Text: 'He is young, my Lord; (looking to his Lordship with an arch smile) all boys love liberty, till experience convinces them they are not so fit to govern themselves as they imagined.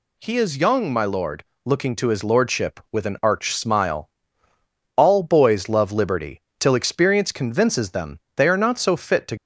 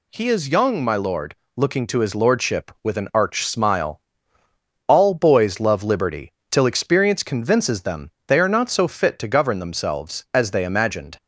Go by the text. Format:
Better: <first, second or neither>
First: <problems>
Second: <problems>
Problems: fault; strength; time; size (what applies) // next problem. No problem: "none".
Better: second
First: pauses between "them" and "they"; slight; at 8.1 s; 0.18 s long // stops before "govern themselves as they imagined"; at 9.3 s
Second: pauses between "them" and "they"; slight; at 8.0 s; 0.18 s long